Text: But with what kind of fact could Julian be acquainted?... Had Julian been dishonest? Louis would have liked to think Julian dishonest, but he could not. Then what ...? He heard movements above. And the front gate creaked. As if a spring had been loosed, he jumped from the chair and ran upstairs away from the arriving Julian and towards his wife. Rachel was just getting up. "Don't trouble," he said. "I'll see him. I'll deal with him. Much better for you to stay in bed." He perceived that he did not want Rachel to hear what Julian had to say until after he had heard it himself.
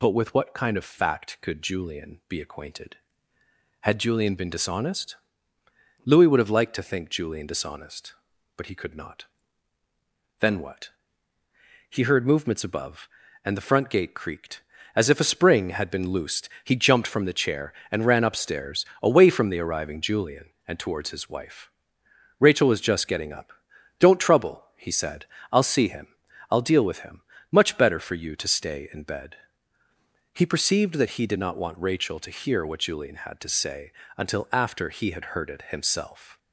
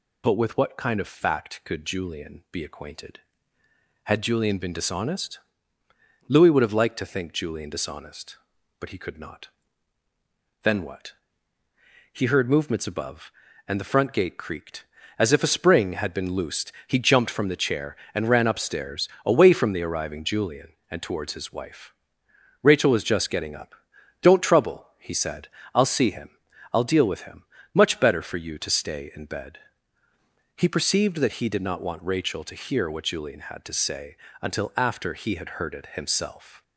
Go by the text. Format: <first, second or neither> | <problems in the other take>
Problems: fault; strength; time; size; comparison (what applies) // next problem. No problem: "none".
neither | pauses between "upstairs" and "away"; slight; the same in both // pauses between "say" and "until"; slight; the same in both